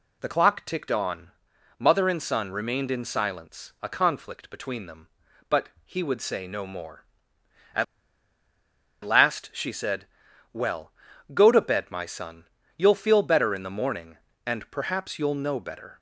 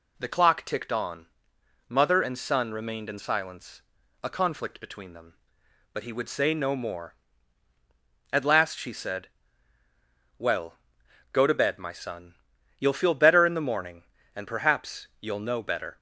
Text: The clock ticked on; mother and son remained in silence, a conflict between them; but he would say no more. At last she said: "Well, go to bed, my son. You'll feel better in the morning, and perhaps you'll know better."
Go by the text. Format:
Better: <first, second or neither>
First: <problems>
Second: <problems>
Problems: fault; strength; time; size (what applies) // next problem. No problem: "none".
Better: second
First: pauses between "but" and "he"; slight; at 5.6 s; 0.16 s long // pauses between "At" and "last"; at 7.8 s; 1.2 s long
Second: none